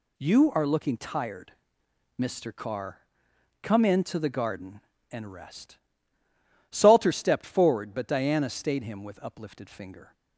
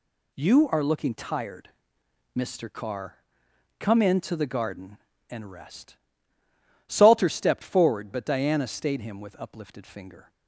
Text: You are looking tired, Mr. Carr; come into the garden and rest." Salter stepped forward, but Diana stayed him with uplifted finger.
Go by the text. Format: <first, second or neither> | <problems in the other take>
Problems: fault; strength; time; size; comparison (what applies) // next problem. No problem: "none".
neither | none